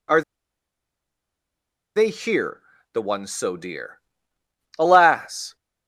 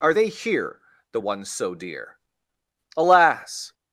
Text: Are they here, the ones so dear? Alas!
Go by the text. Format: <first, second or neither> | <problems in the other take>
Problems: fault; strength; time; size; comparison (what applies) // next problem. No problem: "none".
second | pauses between "Are" and "they"; strong; at 0.2 s; 1.7 s long